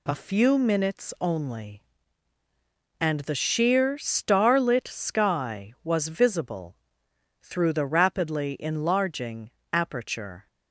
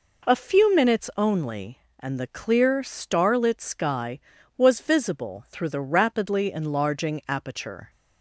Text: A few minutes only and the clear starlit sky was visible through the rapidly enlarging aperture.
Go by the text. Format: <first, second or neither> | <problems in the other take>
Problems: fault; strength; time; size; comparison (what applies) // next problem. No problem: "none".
second | says "sheer" for "clear"; at 3.3 s // pauses between "visible" and "through"; noticeable; at 6.7 s; 0.66 s long // pauses between "enlarging" and "aperture"; slight; at 9.5 s; 0.22 s long